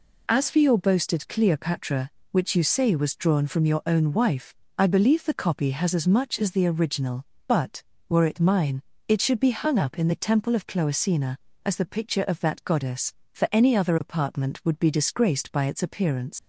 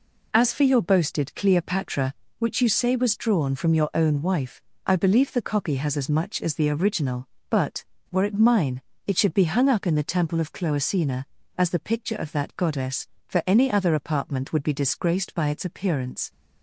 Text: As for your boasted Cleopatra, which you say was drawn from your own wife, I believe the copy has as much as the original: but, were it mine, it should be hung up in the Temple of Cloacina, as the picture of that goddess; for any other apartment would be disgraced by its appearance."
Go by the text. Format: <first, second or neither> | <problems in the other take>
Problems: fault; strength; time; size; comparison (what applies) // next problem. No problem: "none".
second | leaves "appearance" unfinished; at 16.3 s; 90 ms